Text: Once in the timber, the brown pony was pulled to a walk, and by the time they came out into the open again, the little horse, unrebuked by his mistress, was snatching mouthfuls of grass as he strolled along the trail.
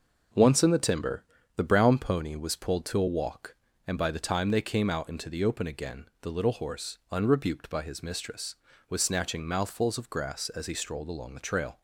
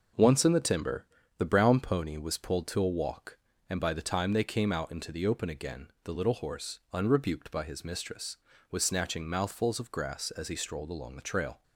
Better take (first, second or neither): neither